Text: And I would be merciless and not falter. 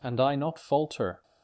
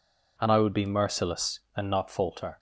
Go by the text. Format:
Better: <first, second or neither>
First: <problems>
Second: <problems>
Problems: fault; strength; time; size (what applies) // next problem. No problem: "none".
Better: second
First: skips "would be merciless and"; at 0.3 s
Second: none